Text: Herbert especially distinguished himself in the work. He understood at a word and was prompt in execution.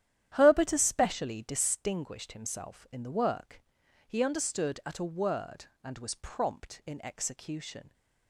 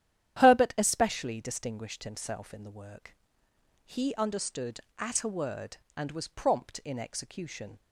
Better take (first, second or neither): neither